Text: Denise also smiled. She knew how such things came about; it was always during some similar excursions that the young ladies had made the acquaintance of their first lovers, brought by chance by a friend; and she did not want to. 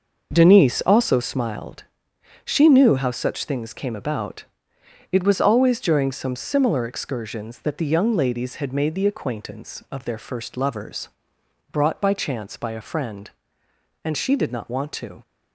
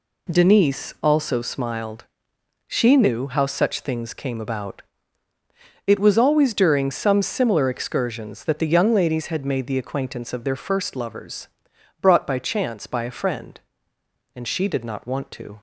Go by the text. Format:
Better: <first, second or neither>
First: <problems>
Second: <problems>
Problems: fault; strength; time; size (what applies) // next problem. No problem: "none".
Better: second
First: starts louder than the rest; noticeable; until 1.3 s; 6 dB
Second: none